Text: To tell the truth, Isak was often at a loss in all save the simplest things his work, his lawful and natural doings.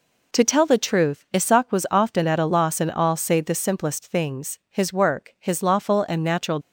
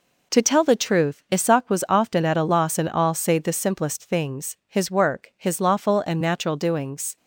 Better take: second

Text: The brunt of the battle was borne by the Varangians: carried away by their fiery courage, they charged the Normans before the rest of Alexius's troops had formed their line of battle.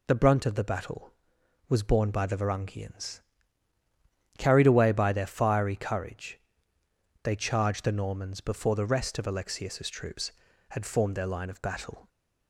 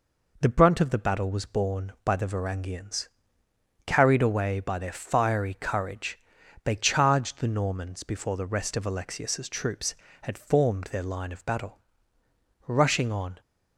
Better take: first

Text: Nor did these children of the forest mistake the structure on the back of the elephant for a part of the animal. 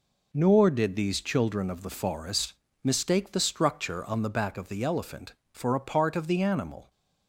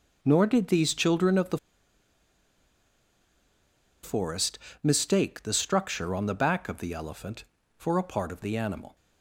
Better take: first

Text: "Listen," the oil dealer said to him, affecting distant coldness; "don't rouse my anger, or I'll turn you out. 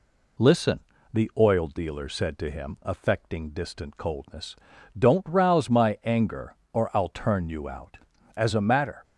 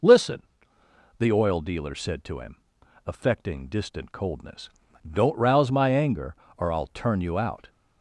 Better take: second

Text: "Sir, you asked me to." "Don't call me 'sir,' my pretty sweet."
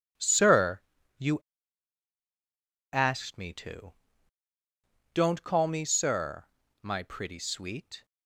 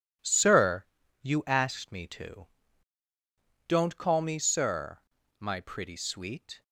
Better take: second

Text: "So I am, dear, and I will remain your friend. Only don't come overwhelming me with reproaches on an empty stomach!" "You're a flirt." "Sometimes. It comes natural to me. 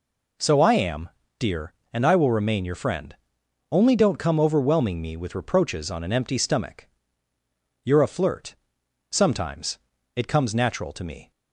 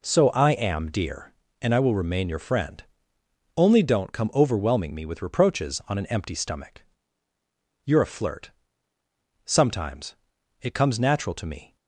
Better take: neither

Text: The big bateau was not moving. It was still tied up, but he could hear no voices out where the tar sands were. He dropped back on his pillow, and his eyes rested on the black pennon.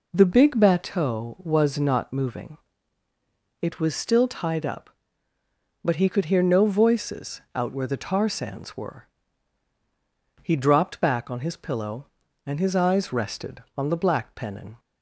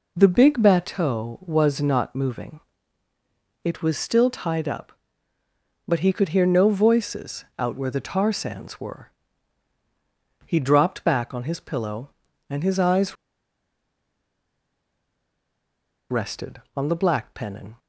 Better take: first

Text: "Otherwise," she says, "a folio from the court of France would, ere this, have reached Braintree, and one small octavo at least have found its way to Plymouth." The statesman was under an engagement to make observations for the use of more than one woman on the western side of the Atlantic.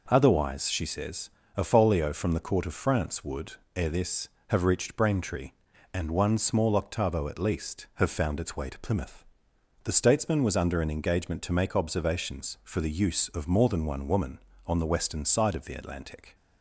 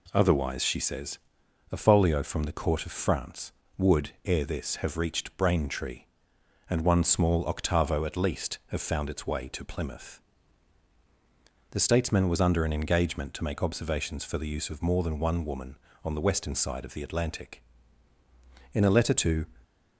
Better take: first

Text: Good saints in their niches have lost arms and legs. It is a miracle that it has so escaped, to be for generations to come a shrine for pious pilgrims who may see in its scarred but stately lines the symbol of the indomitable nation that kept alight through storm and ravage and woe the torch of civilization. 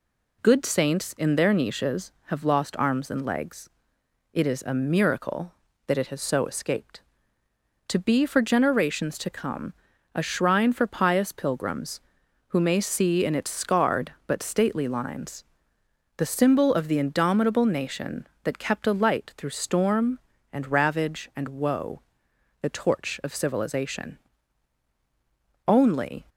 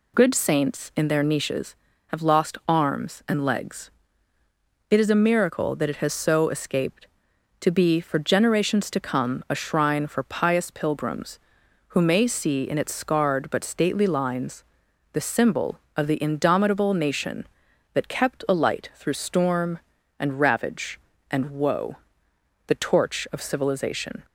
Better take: second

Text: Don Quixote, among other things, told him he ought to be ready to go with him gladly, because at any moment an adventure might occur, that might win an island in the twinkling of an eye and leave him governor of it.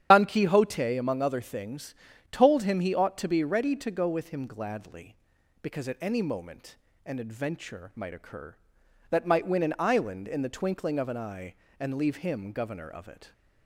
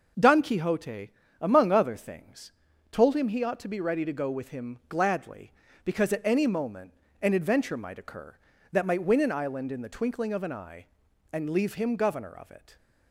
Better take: second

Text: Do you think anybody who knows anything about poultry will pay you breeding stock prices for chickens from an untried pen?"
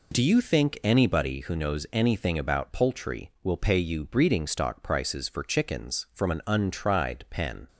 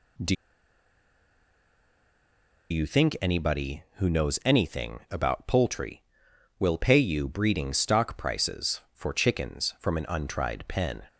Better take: first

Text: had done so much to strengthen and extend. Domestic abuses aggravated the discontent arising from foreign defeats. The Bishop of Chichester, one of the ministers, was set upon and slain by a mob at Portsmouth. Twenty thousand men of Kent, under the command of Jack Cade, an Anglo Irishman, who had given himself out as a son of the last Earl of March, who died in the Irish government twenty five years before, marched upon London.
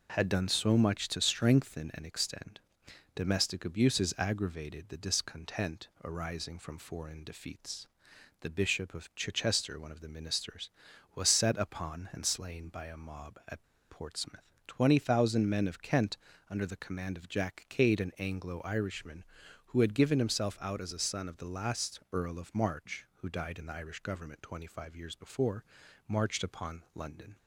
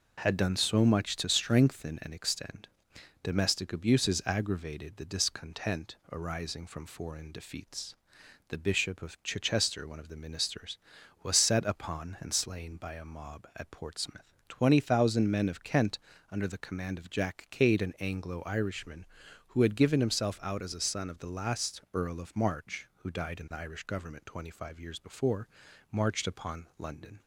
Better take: second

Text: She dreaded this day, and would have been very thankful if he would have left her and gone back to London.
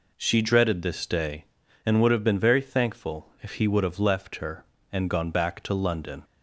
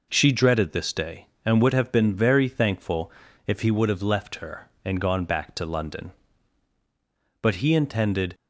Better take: first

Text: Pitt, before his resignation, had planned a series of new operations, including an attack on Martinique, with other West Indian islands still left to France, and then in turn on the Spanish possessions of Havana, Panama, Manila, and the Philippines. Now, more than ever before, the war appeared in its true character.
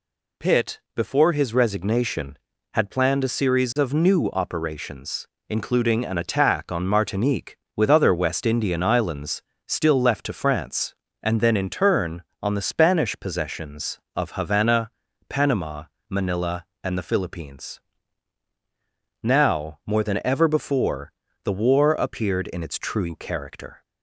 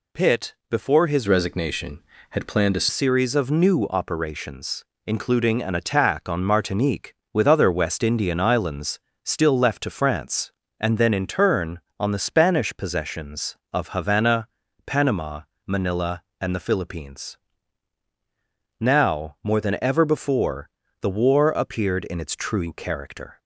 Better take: first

